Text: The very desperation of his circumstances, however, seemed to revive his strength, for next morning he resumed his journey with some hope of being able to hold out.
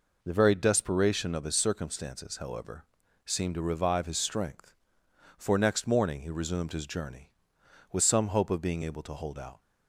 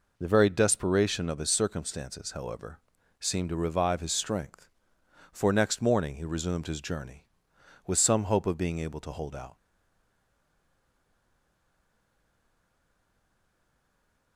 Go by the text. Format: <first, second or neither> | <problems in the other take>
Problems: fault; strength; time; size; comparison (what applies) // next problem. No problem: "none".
first | stays silent after the last word; strong; from 9.5 s on; 4.8 s long